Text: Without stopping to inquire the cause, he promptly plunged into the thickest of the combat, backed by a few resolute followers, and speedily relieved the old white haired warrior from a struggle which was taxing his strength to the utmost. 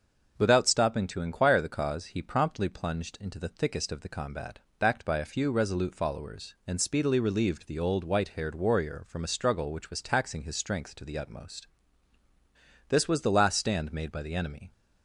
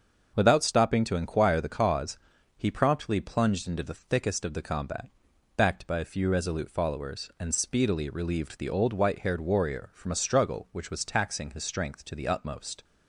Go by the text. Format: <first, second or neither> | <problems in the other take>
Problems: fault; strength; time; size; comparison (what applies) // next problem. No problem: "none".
second | starts louder than the rest; until 1.4 s; 6.5 dB; also in the second // goes on to say "This was the last stand made by the enemy"; strong; from 12.8 s on; 1.8 s long